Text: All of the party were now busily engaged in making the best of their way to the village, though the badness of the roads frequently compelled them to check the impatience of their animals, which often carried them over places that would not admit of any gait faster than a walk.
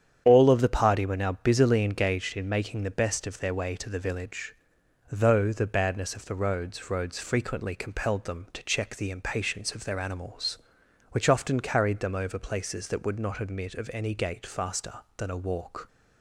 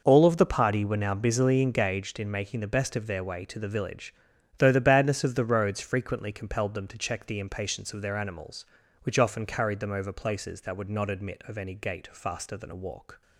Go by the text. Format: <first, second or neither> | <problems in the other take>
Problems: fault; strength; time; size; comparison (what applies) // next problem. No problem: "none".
second | starts louder than the rest; strong; until 1.2 s; 8.5 dB // says "roads" twice; at 6.8 s